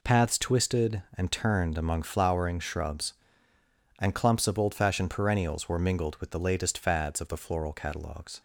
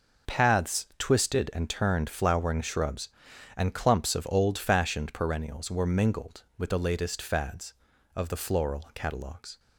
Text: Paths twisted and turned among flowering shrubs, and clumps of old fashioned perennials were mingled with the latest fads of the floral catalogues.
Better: first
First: none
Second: skips "among"; at 2.0 s

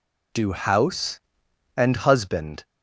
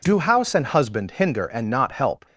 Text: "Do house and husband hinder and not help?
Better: second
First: stops before "hinder and not help"; at 2.6 s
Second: none

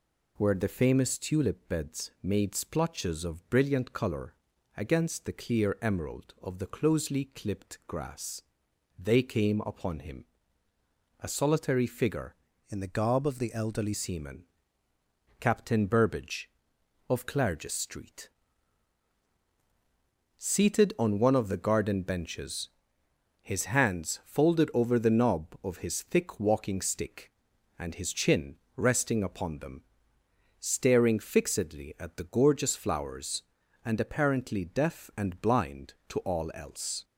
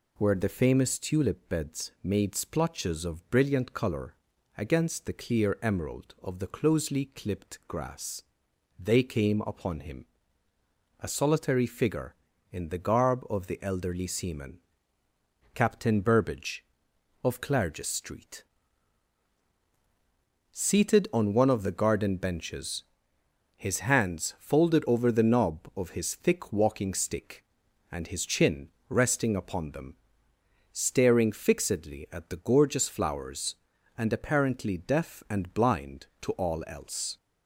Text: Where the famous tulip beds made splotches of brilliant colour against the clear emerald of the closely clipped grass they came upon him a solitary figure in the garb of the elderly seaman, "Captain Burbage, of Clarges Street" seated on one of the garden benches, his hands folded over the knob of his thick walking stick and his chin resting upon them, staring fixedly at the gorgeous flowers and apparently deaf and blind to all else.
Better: second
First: pauses between "colour" and "against"; at 4.3 s; 0.42 s long // pauses between "grass" and "they"; noticeable; at 8.4 s; 0.56 s long // pauses between "him" and "a"; noticeable; at 10.2 s; 0.94 s long // changes voice from "in" to "elderly"; from 12.6 to 13.9 s; 1.3 s long // pauses between "Street" and "seated"; strong; at 18.2 s; 2.0 s long // pauses between "chin" and "resting"; slight; at 28.5 s; 0.18 s long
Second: pauses between "colour" and "against"; at 4.1 s; 0.42 s long // pauses between "grass" and "they"; noticeable; at 8.2 s; 0.56 s long // pauses between "him" and "a"; noticeable; at 10.0 s; 0.93 s long // pauses between "Street" and "seated"; strong; at 18.4 s; 2.0 s long // pauses between "chin" and "resting"; slight; at 28.7 s; 0.18 s long

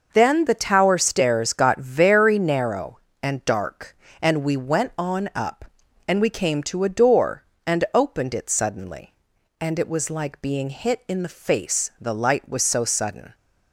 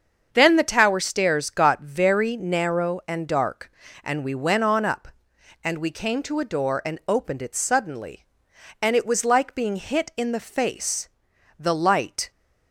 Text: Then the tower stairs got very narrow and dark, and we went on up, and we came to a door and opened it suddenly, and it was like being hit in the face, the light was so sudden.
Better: first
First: none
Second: starts louder than the rest; until 1.3 s; 7 dB // stops before "was so sudden"; at 12.3 s

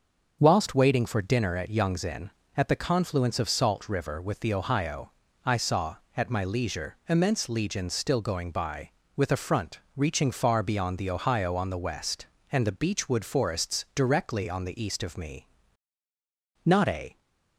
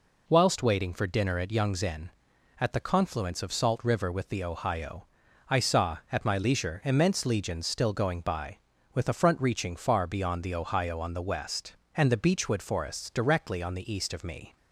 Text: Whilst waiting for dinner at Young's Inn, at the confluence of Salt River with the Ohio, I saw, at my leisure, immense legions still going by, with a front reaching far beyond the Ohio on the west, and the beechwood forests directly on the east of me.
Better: second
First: starts louder than the rest; until 1.4 s; 6 dB // pauses between "front" and "reaching"; slight; at 9.8 s; 0.16 s long // goes on to say "Not a"; from 16.6 s on; 0.54 s long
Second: none

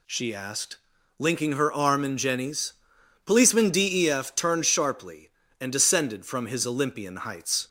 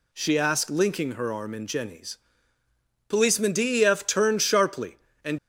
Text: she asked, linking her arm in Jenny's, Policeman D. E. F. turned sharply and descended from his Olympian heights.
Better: first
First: none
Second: stops before "descended from his Olympian heights"; at 5.3 s

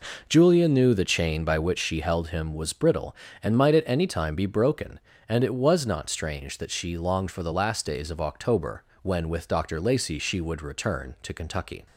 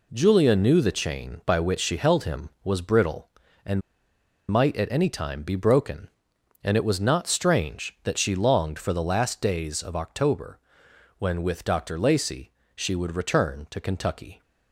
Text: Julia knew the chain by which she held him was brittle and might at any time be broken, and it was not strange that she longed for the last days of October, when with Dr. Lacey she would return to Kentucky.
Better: first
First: none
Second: pauses between "and" and "might"; noticeable; at 3.8 s; 0.70 s long // pauses between "Lacey" and "she"; slight; at 12.5 s; 0.24 s long

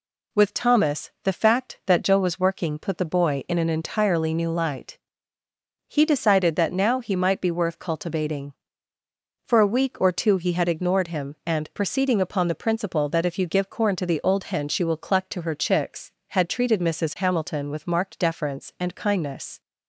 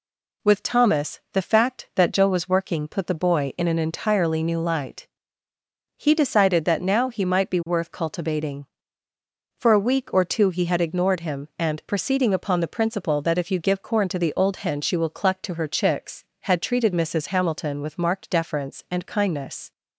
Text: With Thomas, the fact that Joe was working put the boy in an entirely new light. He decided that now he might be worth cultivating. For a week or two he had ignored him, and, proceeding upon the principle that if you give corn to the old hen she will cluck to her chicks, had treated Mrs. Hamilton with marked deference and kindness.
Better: neither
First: none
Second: none

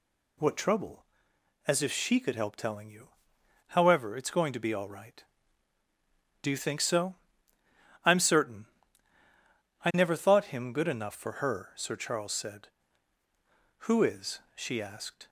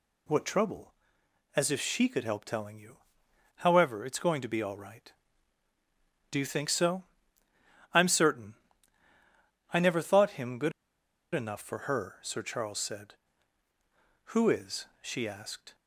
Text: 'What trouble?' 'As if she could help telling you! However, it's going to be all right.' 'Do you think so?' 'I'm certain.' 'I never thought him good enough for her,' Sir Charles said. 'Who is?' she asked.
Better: first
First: none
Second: pauses between "good" and "enough"; noticeable; at 10.7 s; 0.63 s long

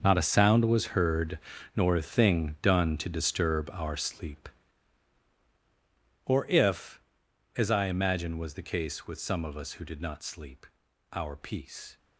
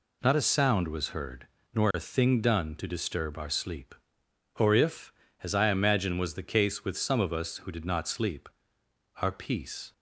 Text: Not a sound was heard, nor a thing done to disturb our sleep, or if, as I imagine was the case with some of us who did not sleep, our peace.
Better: second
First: gets quieter; strong; throughout; 14 dB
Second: none

